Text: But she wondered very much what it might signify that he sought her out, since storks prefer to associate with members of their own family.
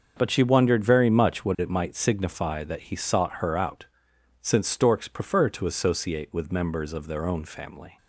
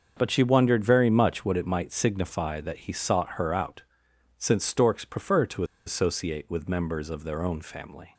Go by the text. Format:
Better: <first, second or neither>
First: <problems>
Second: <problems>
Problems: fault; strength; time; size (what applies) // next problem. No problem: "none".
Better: first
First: starts louder than the rest; until 1.1 s; 6.5 dB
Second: starts louder than the rest; until 1.1 s; 6.5 dB // pauses between "to" and "associate"; slight; at 5.6 s; 0.22 s long